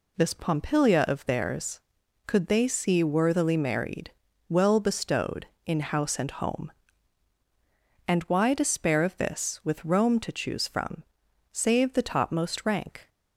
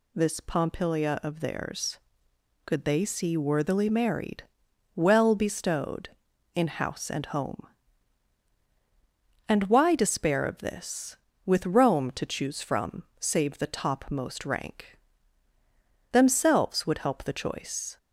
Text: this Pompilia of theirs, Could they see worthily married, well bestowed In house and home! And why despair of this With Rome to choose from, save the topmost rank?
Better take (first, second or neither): first